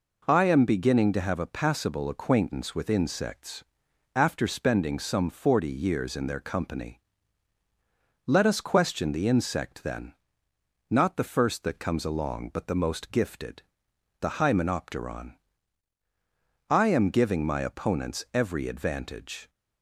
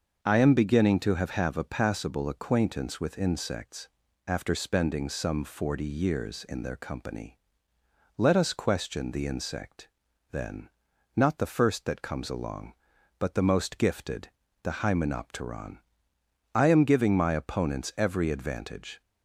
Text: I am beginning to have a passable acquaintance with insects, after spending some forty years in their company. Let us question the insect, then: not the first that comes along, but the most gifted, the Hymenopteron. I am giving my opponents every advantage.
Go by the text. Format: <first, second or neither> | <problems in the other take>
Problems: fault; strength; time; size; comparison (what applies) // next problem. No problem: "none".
first | starts louder than the rest; until 1.2 s; 6 dB // says "have" twice; at 1.3 s